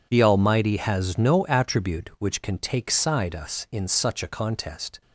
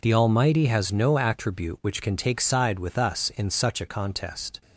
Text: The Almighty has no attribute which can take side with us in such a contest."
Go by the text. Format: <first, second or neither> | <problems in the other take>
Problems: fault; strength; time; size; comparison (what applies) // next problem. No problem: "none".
second | skips "with"; at 3.3 s